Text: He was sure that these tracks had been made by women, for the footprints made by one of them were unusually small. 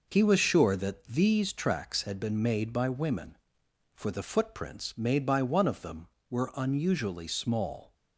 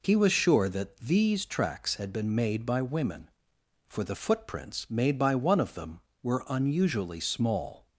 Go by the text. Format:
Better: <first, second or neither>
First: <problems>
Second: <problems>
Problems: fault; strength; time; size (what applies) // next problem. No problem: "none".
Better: second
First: gets quieter; noticeable; throughout; 4.5 dB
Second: none